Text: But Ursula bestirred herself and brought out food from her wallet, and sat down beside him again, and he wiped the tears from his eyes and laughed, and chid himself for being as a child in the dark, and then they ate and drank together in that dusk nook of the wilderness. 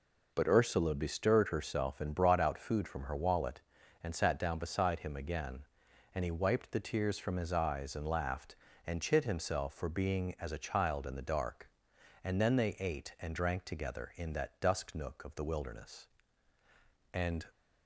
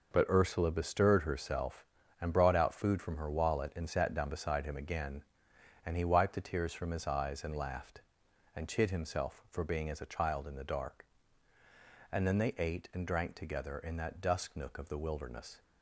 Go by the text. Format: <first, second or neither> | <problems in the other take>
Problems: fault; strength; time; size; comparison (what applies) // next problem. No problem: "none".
second | goes on to say "And"; slight; from 17.1 s on; 0.32 s long